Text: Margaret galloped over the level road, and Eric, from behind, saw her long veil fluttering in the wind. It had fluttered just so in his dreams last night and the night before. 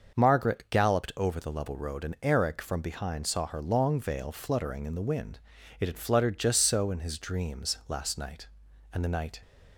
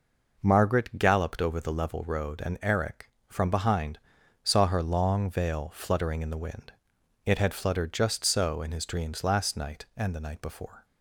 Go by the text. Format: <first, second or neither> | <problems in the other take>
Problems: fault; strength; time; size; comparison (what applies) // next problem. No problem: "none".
second | starts louder than the rest; noticeable; until 1.2 s; 6 dB // stops before "before"; at 9.4 s